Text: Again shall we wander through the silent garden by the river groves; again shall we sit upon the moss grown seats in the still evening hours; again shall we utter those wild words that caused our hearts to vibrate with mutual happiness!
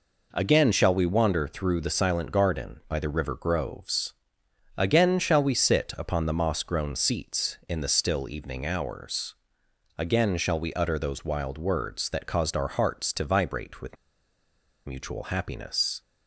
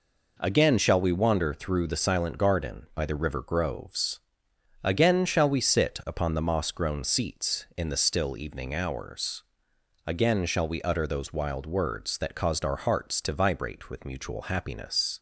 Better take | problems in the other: second | pauses between "with" and "mutual"; noticeable; at 13.9 s; 0.90 s long

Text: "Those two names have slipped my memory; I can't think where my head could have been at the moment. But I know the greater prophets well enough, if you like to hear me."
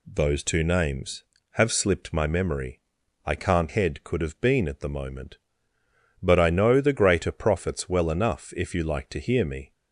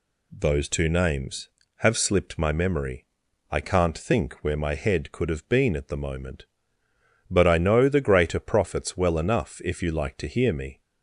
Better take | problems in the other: second | skips "think where my"; at 3.6 s

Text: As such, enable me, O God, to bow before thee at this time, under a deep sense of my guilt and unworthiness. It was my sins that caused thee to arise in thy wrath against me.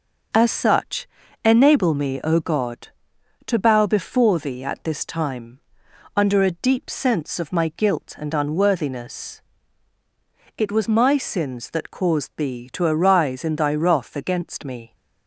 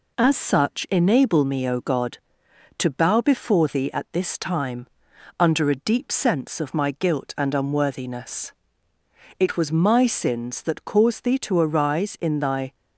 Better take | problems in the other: first | stops before "wrath against me"; at 12.7 s

